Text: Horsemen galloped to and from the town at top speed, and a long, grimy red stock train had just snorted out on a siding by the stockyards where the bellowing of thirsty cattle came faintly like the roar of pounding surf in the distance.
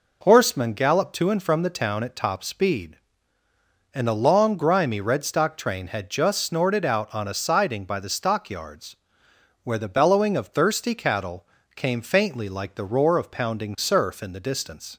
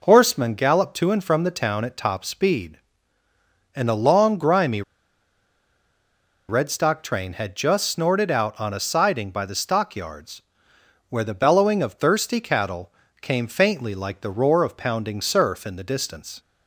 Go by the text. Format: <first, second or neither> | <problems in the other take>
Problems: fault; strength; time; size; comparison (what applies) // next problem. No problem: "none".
first | pauses between "grimy" and "red"; strong; at 4.8 s; 1.6 s long // pauses between "stockyards" and "where"; noticeable; at 10.3 s; 0.70 s long; noticeable in the first // pauses between "cattle" and "came"; slight; at 12.8 s; 0.30 s long; slight in the first